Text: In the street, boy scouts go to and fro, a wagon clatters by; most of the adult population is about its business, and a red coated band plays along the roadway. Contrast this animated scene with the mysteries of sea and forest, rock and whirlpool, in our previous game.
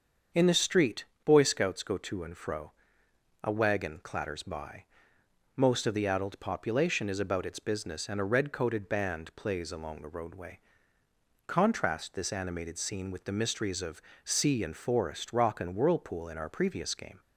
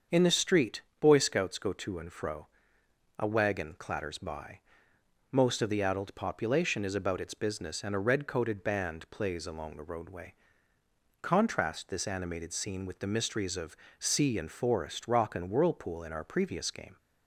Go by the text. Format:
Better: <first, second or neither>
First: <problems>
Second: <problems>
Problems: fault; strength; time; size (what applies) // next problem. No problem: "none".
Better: neither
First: starts louder than the rest; until 1.5 s; 7 dB // pauses between "of" and "sea"; slight; at 14.0 s; 0.20 s long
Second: starts louder than the rest; until 1.2 s; 7 dB // pauses between "of" and "sea"; slight; at 13.7 s; 0.20 s long